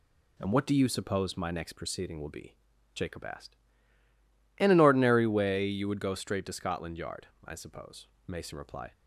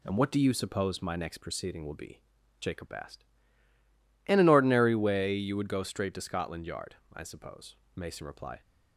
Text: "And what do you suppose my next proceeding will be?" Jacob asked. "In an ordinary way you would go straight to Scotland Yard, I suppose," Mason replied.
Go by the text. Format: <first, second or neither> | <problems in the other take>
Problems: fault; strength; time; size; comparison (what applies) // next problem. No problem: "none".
neither | none